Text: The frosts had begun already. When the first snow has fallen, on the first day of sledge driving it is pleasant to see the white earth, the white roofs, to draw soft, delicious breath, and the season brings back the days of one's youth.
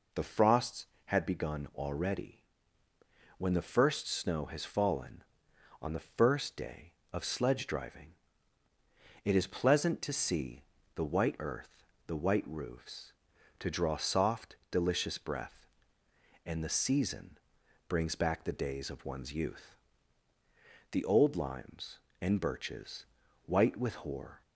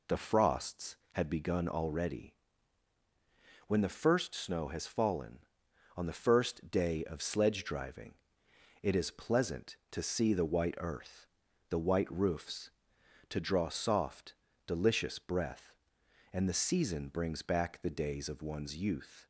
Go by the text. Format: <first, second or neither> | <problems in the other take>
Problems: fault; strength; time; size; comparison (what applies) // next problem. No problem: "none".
second | pauses between "driving" and "it"; at 8.1 s; 1.1 s long; noticeable in the second // pauses between "see" and "the"; slight; at 10.6 s; 0.32 s long // pauses between "season" and "brings"; noticeable; at 17.3 s; 0.48 s long // goes on to say "The old limes and birches white with hoar"; strong; from 20.9 s on; 3.5 s long